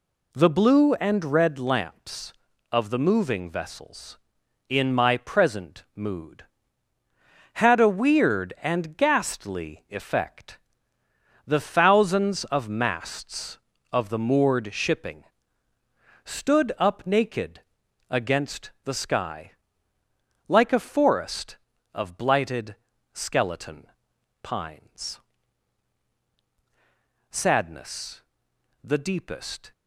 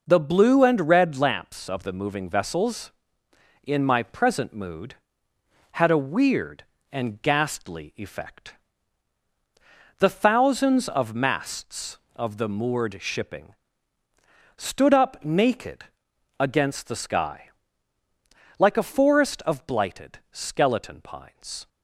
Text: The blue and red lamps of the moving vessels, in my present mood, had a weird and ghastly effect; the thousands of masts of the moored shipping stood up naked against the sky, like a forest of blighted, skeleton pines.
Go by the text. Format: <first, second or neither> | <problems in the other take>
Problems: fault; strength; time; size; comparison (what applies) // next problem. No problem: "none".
second | pauses between "shipping" and "stood"; at 15.2 s; 1.0 s long; also in the second // pauses between "naked" and "against"; noticeable; at 17.6 s; 0.46 s long; noticeable in the second // pauses between "skeleton" and "pines"; at 23.8 s; 1.0 s long // goes on to say "Sadness the deepest"; strong; from 27.3 s on; 2.4 s long